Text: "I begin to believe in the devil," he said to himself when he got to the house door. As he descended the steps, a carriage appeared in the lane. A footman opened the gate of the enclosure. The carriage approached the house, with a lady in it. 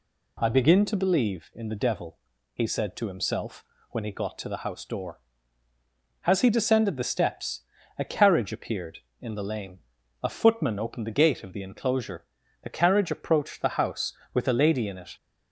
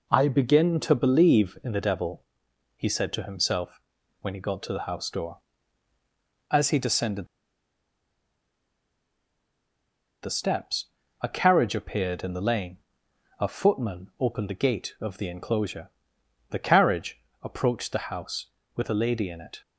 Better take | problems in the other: first | pauses between "himself" and "when"; at 3.8 s; 0.40 s long; slight in the first // pauses between "descended" and "the"; strong; at 7.2 s; 2.9 s long // pauses between "carriage" and "approached"; slight; at 17.2 s; 0.20 s long

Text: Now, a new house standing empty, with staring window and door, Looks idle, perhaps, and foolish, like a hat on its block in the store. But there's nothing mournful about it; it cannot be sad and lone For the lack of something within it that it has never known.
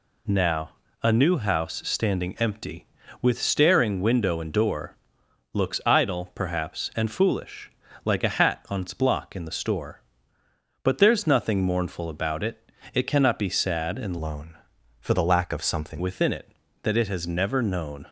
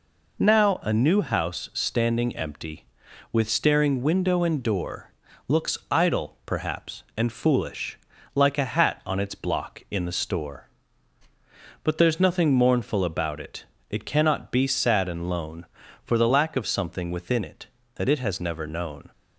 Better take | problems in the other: second | changes voice from "lone" to "something"; from 14.2 to 16.0 s; 1.8 s long

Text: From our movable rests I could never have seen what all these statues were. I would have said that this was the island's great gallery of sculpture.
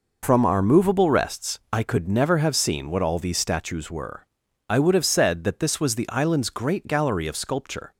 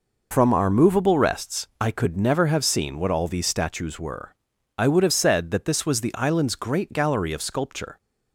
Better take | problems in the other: neither | none

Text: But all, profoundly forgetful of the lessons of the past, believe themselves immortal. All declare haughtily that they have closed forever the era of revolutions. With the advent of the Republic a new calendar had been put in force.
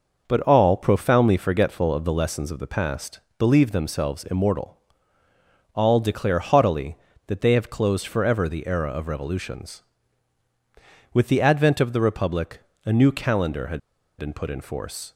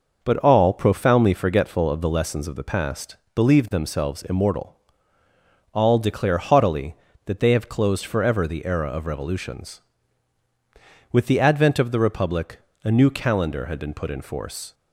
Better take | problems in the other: second | pauses between "Republic" and "a"; slight; at 12.6 s; 0.26 s long; slight in the second // pauses between "had" and "been"; at 13.8 s; 0.39 s long

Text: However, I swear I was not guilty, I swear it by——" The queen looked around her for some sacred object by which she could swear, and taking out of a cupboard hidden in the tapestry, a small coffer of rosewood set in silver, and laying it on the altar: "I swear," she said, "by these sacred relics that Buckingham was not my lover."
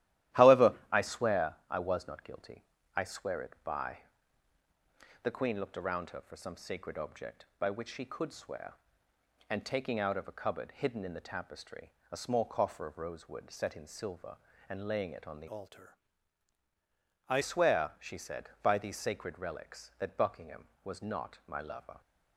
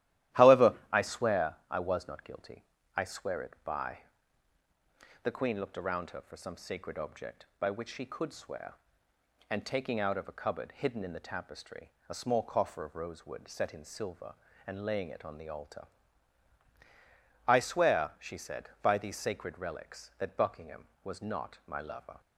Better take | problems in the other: second | starts louder than the rest; strong; until 1.5 s; 14 dB; strong in the second // changes voice from "altar" to "I"; from 15.4 to 17.3 s; 1.9 s long

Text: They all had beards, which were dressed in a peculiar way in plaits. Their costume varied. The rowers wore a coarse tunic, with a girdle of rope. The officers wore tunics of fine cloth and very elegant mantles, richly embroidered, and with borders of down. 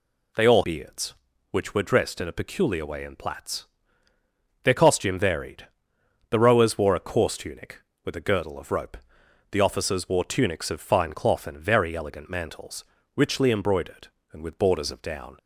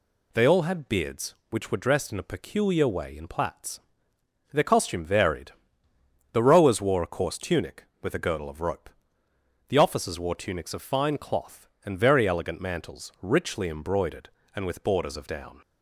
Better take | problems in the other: second | skips "had"; at 0.6 s

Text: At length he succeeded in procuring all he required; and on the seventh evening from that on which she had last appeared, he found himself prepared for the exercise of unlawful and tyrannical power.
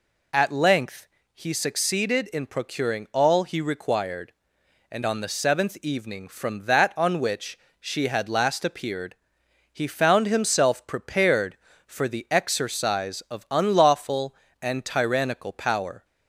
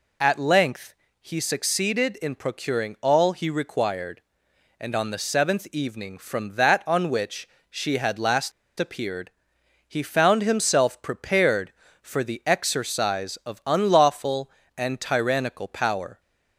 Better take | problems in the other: first | pauses between "length" and "he"; slight; at 0.9 s; 0.26 s long; slight in the first // pauses between "which" and "she"; slight; at 7.4 s; 0.20 s long; slight in the first // pauses between "last" and "appeared"; slight; at 8.5 s; 0.28 s long

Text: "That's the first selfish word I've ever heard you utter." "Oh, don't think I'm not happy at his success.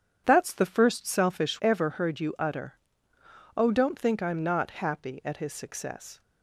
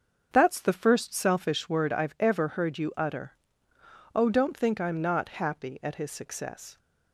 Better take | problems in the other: second | starts louder than the rest; strong; until 1.2 s; 8.5 dB; also in the second // skips "word I've"; at 1.5 s

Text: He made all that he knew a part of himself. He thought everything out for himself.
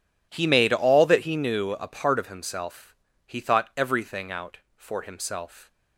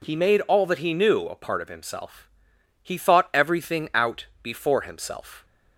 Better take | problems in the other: first | says "before" for "for"; at 4.4 s

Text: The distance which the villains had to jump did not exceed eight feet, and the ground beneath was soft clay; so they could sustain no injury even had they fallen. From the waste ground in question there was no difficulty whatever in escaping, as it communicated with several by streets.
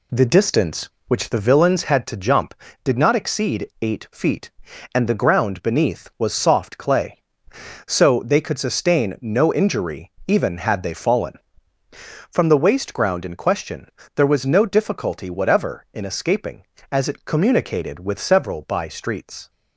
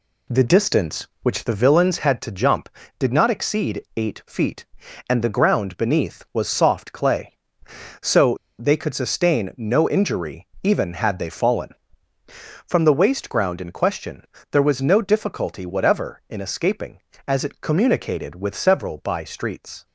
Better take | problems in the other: first | pauses between "so" and "they"; slight; at 8.3 s; 0.23 s long // pauses between "injury" and "even"; slight; at 10.4 s; 0.16 s long; slight in the first // pauses between "question" and "there"; slight; at 14.2 s; 0.26 s long; slight in the first

